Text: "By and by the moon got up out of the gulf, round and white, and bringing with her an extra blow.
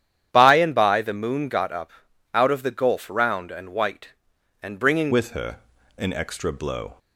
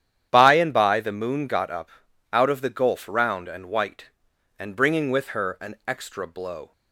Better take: second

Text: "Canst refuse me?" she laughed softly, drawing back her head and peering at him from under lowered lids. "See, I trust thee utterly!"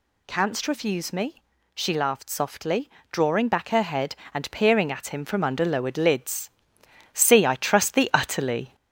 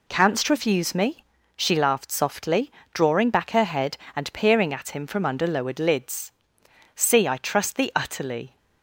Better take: second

